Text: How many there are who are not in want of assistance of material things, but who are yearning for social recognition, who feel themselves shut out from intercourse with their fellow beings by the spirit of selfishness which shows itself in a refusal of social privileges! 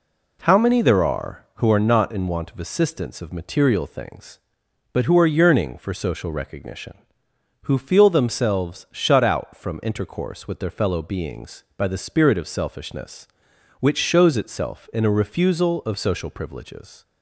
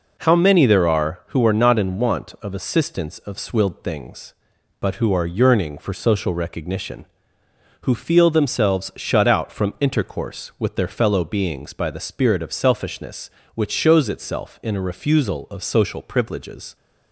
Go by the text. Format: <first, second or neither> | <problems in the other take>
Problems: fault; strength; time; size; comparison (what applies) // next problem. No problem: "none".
first | says "swilled" for "material"; at 3.3 s